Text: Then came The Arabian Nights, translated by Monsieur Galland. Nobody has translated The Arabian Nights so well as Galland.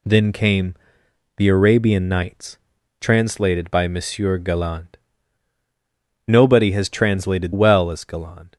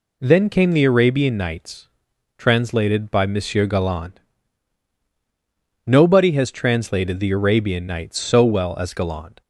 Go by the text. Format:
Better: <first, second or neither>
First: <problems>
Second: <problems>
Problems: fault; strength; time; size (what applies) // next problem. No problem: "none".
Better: second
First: pauses between "came" and "The"; noticeable; at 0.7 s; 0.64 s long // skips "The Arabian Nights so"; at 7.5 s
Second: none